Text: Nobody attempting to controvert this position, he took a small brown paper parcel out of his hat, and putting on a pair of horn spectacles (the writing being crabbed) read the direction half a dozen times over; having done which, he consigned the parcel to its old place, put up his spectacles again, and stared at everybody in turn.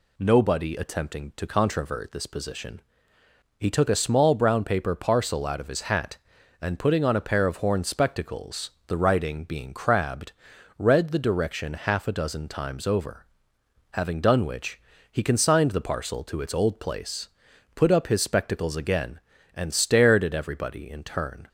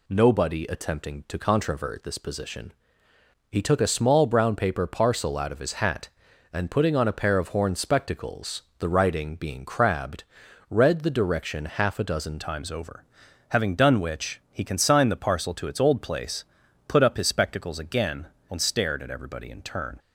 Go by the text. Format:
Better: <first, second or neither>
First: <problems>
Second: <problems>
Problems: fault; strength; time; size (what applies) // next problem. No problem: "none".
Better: first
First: none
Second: changes voice at "times"; from 12.4 s on; 7.5 s long